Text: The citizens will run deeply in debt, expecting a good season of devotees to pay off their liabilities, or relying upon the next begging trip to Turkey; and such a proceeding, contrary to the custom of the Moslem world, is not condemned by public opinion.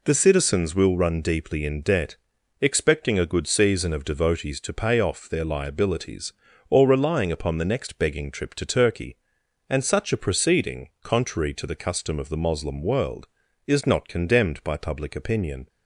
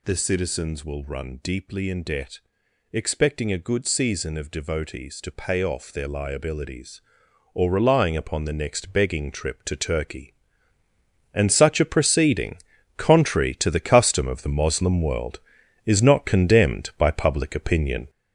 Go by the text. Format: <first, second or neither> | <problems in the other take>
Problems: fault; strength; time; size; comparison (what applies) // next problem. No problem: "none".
first | gets louder; throughout; 7 dB